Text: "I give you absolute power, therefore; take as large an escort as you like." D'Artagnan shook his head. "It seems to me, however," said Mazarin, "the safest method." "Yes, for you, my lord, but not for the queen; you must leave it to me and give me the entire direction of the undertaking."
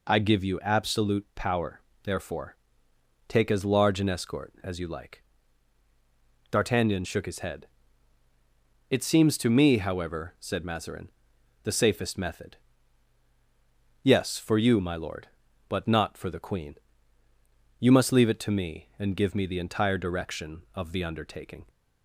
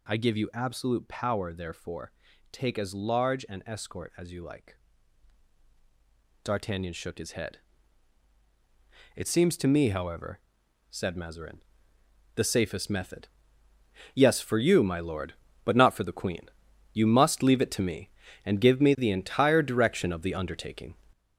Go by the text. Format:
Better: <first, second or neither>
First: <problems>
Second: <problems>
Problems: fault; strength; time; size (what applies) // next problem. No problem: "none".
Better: first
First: none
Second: gets louder; noticeable; throughout; 6 dB